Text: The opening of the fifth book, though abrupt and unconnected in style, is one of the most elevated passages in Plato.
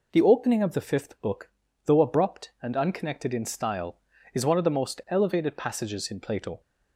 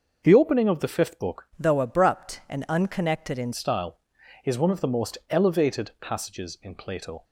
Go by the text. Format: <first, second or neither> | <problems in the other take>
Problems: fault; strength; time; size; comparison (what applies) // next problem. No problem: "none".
first | starts louder than the rest; until 1.2 s; 6 dB // changes voice from "though" to "in"; from 1.5 to 3.5 s; 2.0 s long